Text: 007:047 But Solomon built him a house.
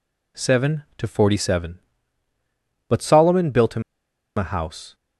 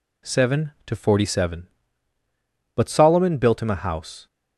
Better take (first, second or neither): second